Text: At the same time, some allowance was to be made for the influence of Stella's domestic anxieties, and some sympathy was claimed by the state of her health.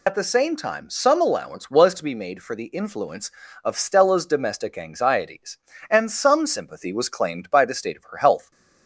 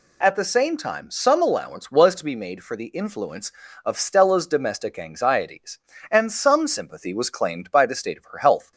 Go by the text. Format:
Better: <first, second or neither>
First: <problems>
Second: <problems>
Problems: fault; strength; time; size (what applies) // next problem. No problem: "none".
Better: second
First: loses the start of "At"; at 0.0 s; 70 ms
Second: none